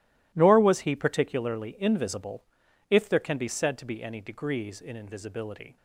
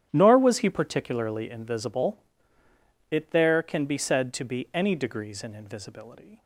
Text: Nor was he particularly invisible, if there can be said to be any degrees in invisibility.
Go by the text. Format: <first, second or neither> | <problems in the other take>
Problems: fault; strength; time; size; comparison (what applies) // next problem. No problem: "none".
first | starts louder than the rest; strong; until 1.1 s; 10 dB // says "it" for "if"; at 3.1 s